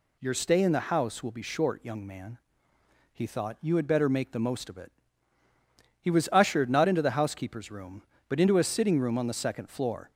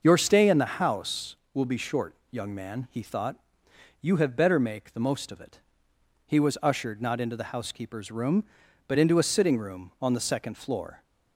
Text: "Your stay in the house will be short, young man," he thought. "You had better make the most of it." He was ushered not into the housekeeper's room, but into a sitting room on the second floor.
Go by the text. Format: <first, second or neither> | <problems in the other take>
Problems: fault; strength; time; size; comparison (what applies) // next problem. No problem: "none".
first | starts louder than the rest; noticeable; until 1.0 s; 6 dB // says "have" for "had"; at 4.1 s